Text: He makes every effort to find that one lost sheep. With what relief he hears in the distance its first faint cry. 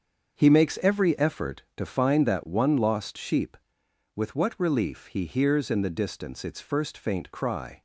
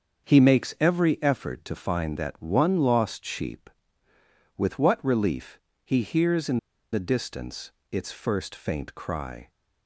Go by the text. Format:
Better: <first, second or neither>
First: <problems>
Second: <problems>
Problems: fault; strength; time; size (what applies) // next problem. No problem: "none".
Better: first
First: starts louder than the rest; until 1.4 s; 7 dB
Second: starts louder than the rest; until 1.3 s; 7 dB // pauses between "relief" and "he"; slight; at 5.5 s; 0.24 s long // pauses between "in" and "the"; slight; at 6.5 s; 0.35 s long // pauses between "distance" and "its"; slight; at 7.7 s; 0.22 s long